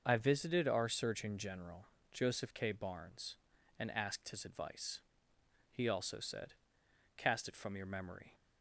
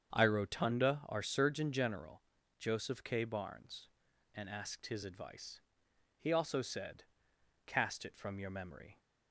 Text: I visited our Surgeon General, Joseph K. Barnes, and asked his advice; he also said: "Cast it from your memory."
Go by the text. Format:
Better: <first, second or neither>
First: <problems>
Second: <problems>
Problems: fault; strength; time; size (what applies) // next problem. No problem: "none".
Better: first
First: starts louder than the rest; until 1.0 s; 6.5 dB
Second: starts louder than the rest; strong; until 1.1 s; 7.5 dB // says "rotunda" for "visited"; at 0.2 s